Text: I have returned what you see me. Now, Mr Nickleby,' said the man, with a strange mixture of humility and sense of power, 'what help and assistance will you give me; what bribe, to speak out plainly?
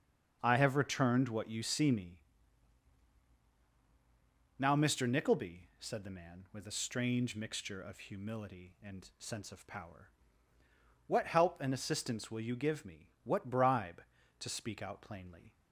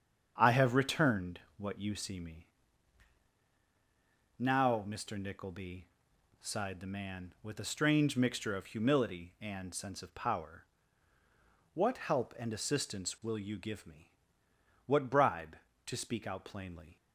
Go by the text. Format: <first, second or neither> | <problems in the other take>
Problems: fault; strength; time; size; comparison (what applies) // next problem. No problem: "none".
first | starts louder than the rest; strong; until 1.3 s; 7.5 dB; also in the first // pauses between "returned" and "what"; slight; at 1.3 s; 0.18 s long // says "sighed" for "said"; at 6.4 s